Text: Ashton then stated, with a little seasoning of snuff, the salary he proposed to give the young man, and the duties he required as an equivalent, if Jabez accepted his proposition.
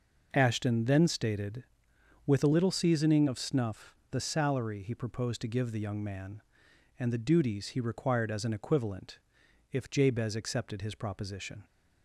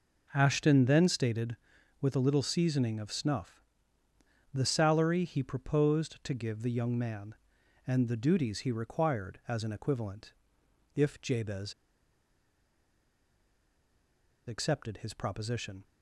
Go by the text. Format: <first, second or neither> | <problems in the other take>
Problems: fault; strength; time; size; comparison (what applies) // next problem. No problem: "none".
first | pauses between "Jabez" and "accepted"; strong; at 11.7 s; 2.7 s long